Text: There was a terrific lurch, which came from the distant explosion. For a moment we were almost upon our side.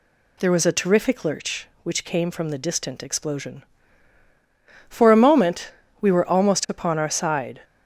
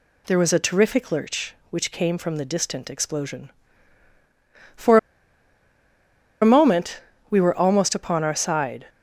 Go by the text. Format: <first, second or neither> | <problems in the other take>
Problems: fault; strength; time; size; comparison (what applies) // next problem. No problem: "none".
first | pauses between "For" and "a"; strong; at 4.9 s; 1.4 s long // pauses between "moment" and "we"; slight; at 7.0 s; 0.30 s long; slight in the first